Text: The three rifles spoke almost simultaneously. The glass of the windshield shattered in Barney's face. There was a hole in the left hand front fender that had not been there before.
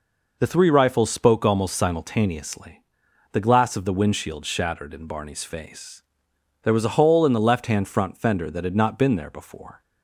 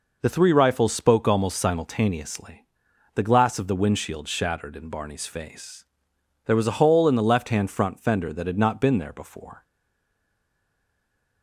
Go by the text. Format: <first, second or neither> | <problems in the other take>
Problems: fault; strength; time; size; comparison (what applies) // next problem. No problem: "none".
first | stays silent after the last word; noticeable; from 9.6 s on; 1.8 s long